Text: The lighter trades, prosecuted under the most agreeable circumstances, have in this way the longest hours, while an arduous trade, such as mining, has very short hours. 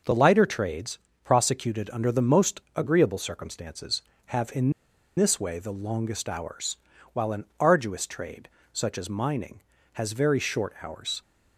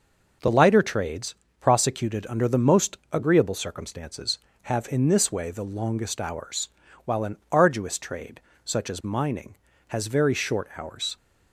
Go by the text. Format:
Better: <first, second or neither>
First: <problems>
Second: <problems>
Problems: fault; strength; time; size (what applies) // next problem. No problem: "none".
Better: second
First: pauses between "most" and "agreeable"; slight; at 2.5 s; 0.16 s long // pauses between "in" and "this"; at 4.7 s; 0.44 s long // pauses between "an" and "arduous"; slight; at 7.4 s; 0.16 s long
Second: pauses between "most" and "agreeable"; slight; at 2.9 s; 0.16 s long // pauses between "an" and "arduous"; slight; at 7.3 s; 0.16 s long